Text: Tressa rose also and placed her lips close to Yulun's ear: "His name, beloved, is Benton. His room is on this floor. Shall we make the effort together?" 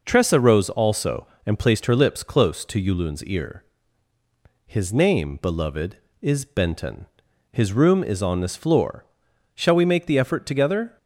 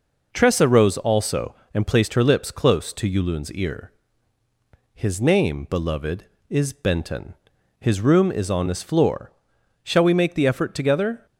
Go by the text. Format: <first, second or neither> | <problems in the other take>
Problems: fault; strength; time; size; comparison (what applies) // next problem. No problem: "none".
neither | none